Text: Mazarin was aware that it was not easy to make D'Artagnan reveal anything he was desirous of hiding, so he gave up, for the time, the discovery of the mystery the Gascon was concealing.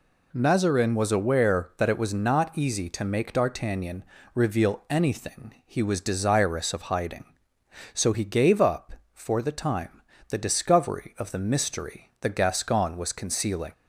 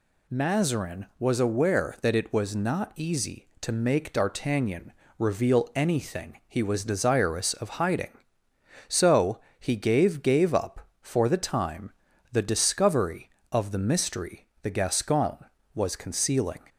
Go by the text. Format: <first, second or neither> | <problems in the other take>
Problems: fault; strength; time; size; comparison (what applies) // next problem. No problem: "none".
first | pauses between "D'Artagnan" and "reveal"; slight; at 4.9 s; 0.26 s long; slight in the first // pauses between "so" and "he"; slight; at 9.3 s; 0.20 s long // says "gave" twice; at 10.2 s // pauses between "mystery" and "the"; slight; at 14.4 s; 0.16 s long